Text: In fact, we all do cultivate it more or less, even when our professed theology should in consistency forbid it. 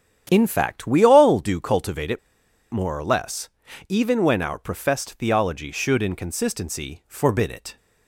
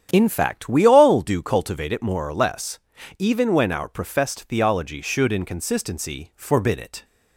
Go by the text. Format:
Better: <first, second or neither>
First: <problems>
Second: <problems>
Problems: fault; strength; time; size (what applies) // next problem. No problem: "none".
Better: second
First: starts louder than the rest; strong; until 1.3 s; 9 dB // pauses between "it" and "more"; noticeable; at 2.1 s; 0.52 s long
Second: starts louder than the rest; strong; until 1.1 s; 9 dB